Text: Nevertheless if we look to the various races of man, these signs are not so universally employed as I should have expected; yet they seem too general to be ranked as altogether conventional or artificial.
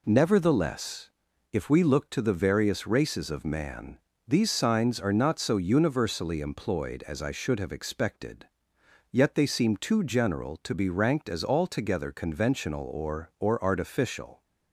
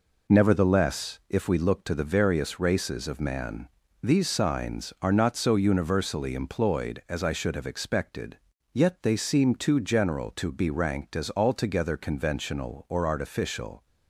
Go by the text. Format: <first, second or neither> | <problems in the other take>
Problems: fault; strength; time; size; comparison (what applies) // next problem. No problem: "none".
second | pauses between "Nevertheless" and "if"; at 1.0 s; 0.42 s long // says "or" twice; at 13.3 s